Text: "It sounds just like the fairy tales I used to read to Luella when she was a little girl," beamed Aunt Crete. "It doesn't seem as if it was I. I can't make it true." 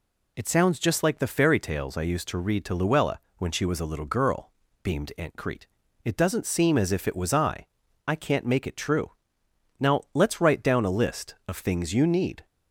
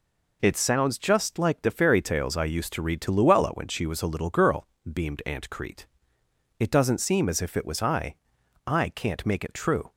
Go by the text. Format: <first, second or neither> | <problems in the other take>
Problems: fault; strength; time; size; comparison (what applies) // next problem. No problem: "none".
second | pauses between "Luella" and "when"; slight; at 3.1 s; 0.20 s long // goes on to say "Now let's write down a list of things you need"; strong; from 9.7 s on; 2.6 s long